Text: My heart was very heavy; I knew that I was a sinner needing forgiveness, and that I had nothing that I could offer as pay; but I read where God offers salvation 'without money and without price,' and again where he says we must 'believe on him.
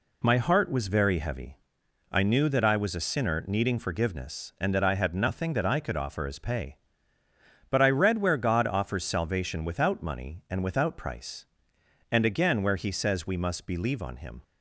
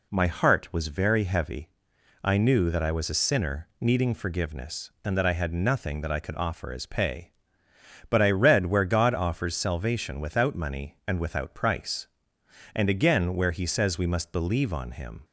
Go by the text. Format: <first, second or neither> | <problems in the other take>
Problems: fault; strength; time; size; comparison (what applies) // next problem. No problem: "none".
neither | none